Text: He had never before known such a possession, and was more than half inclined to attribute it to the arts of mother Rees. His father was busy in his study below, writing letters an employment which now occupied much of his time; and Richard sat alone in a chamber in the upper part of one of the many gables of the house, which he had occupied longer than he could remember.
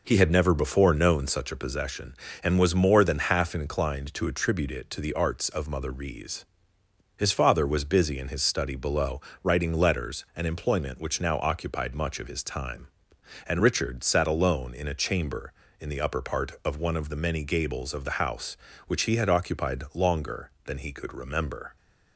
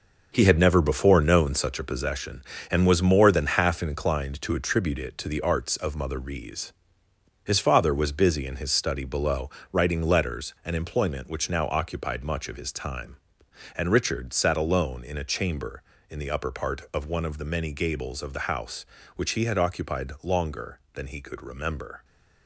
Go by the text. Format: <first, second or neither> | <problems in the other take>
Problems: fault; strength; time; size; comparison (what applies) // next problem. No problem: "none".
first | gets quieter; strong; throughout; 8 dB